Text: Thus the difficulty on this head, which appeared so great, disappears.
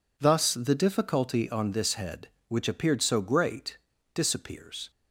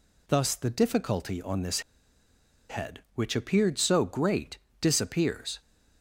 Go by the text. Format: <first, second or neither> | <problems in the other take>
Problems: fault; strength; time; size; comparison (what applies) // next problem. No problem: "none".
first | pauses between "this" and "head"; noticeable; at 1.7 s; 0.89 s long